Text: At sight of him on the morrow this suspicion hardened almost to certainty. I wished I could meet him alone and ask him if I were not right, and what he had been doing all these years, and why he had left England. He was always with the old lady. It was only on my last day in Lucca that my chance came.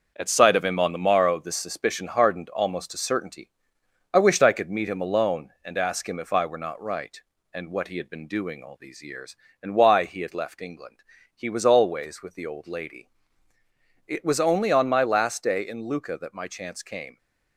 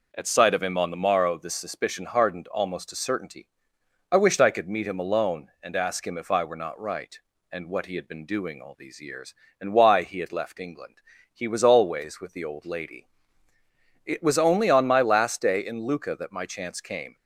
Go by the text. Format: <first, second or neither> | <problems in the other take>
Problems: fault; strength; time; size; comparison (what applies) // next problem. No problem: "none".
second | gets quieter; throughout; 6 dB